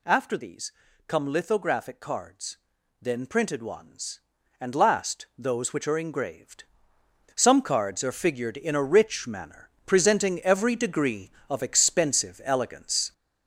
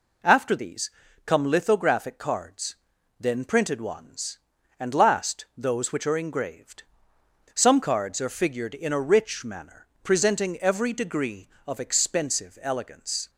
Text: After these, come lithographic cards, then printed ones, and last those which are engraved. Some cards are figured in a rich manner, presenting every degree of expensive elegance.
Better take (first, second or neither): second